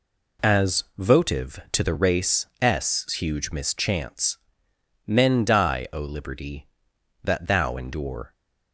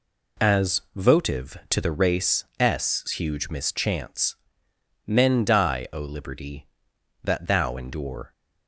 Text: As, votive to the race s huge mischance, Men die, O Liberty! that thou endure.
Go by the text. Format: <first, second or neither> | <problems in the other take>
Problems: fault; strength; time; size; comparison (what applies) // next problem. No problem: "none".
neither | pauses between "race" and "s"; slight; the same in both